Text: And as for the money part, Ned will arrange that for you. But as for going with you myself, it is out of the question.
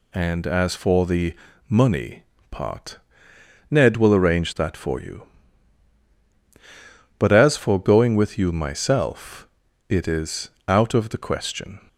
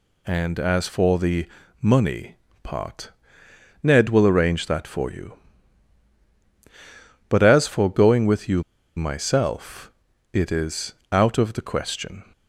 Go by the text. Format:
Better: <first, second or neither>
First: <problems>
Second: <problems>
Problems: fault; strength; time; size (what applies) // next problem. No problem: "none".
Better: first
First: pauses between "the" and "money"; slight; at 1.3 s; 0.34 s long // pauses between "money" and "part"; slight; at 2.2 s; 0.26 s long // pauses between "is" and "out"; slight; at 10.4 s; 0.18 s long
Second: pauses between "the" and "money"; slight; at 1.4 s; 0.34 s long // pauses between "money" and "part"; slight; at 2.3 s; 0.26 s long // pauses between "you" and "myself"; slight; at 8.6 s; 0.34 s long // pauses between "is" and "out"; slight; at 10.9 s; 0.18 s long